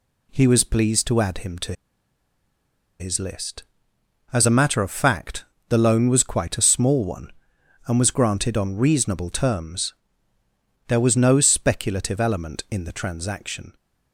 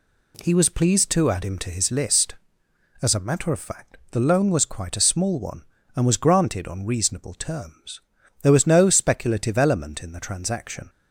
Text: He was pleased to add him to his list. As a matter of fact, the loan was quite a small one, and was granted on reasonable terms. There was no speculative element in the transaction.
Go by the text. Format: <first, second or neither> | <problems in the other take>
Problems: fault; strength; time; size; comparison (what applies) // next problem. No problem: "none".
second | pauses between "to" and "his"; strong; at 1.7 s; 1.2 s long